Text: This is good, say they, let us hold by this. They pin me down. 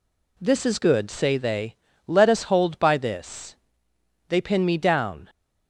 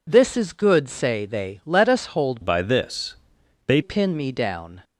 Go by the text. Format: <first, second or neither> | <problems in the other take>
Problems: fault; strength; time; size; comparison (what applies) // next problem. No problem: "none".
first | changes voice from "by" to "They"; from 2.4 to 3.7 s; 1.3 s long